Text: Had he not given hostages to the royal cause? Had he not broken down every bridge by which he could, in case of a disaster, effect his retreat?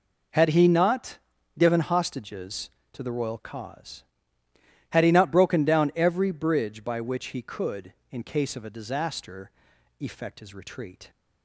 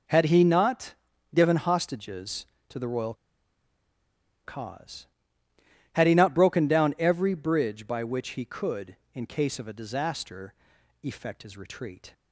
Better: first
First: pauses between "not" and "given"; at 1.1 s; 0.40 s long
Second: pauses between "not" and "given"; at 0.9 s; 0.40 s long // pauses between "royal" and "cause"; strong; at 3.1 s; 1.3 s long

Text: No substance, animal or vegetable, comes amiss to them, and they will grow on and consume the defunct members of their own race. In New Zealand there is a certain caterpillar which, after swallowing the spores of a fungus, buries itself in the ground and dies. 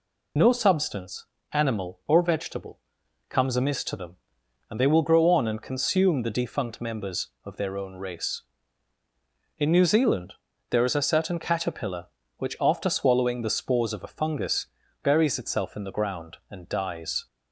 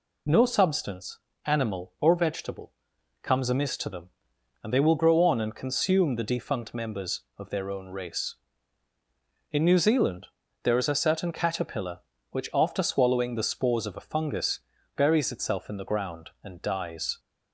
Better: second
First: loses the start of "No"; at 0.3 s; 25 ms // pauses between "Zealand" and "there"; at 10.3 s; 0.38 s long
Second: pauses between "Zealand" and "there"; at 10.2 s; 0.38 s long

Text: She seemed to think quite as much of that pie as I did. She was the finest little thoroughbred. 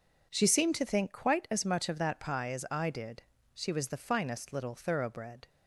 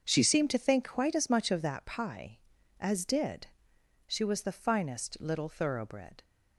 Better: first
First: none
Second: starts louder than the rest; until 1.0 s; 6.5 dB // skips "I"; at 3.0 s

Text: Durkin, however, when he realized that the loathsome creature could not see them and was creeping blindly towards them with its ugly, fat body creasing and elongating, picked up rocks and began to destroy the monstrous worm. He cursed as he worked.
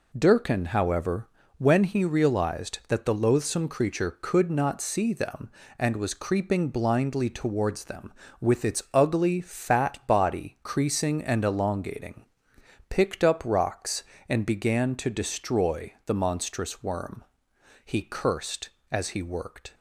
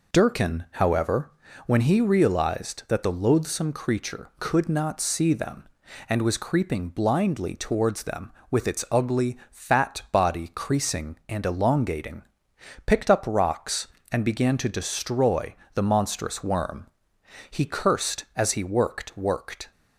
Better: first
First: none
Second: pauses between "destroy" and "the"; slight; at 15.5 s; 0.20 s long // says "worked" twice; at 19.1 s

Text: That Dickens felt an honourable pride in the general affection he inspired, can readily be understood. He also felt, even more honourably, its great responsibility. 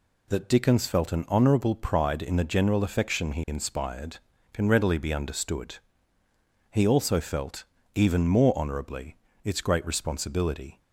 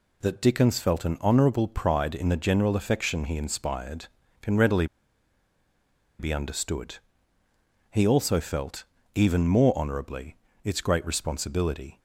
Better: first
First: none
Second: pauses between "readily" and "be"; strong; at 4.8 s; 1.3 s long

